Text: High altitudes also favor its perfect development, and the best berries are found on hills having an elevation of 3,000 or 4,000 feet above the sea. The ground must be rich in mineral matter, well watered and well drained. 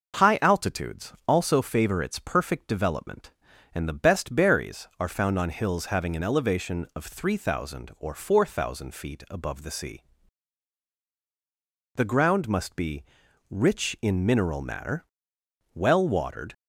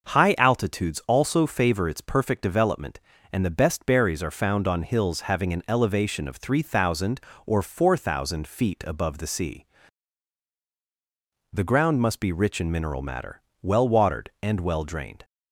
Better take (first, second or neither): second